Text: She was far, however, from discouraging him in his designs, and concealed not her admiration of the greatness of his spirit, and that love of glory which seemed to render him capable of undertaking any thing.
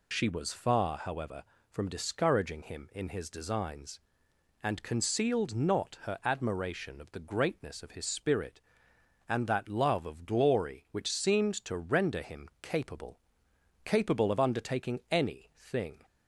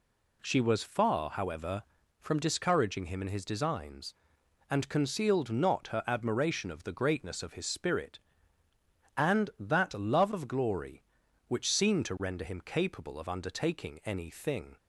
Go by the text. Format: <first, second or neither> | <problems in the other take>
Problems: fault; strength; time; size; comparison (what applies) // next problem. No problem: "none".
second | says "capable" twice; at 13.8 s